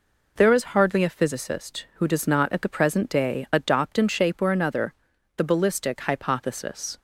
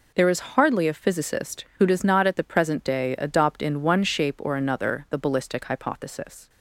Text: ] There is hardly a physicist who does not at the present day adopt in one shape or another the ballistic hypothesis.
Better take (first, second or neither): second